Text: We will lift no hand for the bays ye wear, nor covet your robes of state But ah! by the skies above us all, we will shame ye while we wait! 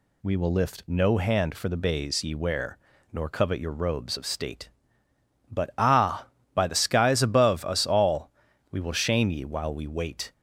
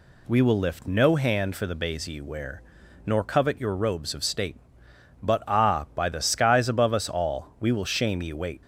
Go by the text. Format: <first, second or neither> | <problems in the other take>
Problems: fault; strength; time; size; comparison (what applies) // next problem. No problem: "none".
first | skips "while we"; at 8.3 s